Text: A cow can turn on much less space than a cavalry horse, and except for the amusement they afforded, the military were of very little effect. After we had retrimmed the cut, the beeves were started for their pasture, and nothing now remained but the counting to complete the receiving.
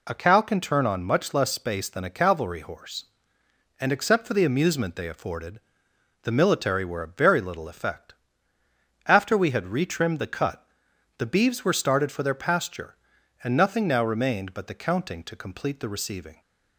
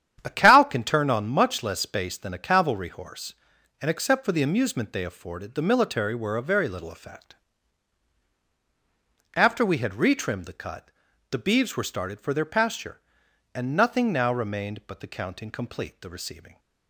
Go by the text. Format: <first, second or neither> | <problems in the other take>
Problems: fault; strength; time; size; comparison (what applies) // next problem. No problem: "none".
first | starts louder than the rest; strong; until 1.2 s; 9.5 dB // skips "to"; at 15.5 s